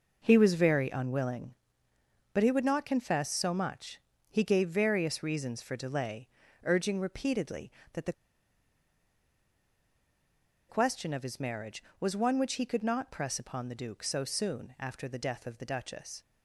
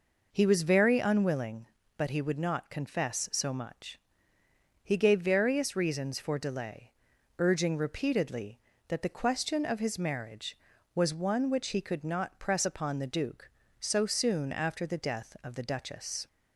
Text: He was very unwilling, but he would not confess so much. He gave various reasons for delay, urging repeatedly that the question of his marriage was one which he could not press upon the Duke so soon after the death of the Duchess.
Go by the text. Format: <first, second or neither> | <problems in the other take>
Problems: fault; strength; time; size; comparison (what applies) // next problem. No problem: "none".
second | pauses between "the" and "question"; strong; at 8.1 s; 2.5 s long